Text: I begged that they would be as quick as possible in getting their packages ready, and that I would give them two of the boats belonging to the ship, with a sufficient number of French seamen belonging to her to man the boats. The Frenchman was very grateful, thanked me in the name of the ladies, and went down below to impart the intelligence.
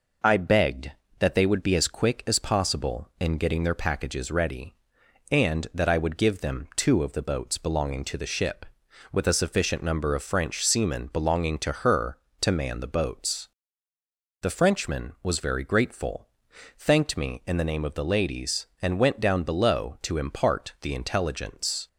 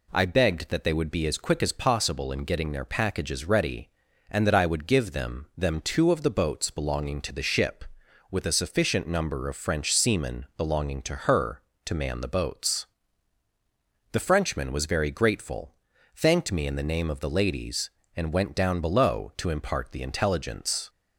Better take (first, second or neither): first